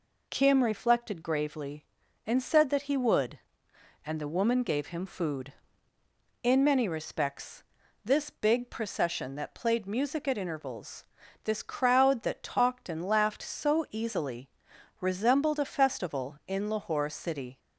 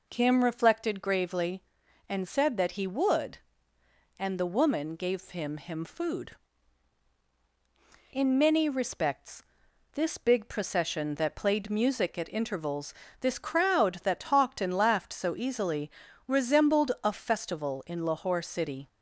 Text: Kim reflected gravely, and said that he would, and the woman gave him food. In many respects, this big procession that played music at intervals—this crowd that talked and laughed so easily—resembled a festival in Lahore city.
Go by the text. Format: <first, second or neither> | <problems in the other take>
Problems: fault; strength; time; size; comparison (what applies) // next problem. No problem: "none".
first | says "him" twice; at 5.5 s